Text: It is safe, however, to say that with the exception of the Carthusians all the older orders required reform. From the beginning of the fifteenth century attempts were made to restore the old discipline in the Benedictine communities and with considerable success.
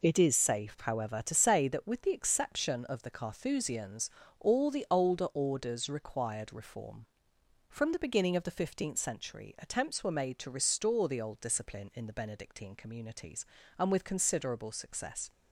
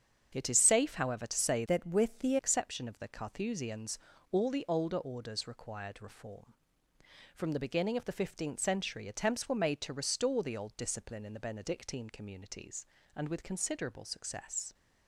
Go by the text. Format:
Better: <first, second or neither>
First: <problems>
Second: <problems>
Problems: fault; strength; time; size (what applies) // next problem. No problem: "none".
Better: first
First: pauses between "Carthusians" and "all"; slight; at 4.1 s; 0.28 s long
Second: starts louder than the rest; strong; until 1.3 s; 7.5 dB // changes voice from "that" to "the"; from 1.6 to 2.3 s; 0.7 s long // pauses between "Carthusians" and "all"; slight; at 3.9 s; 0.34 s long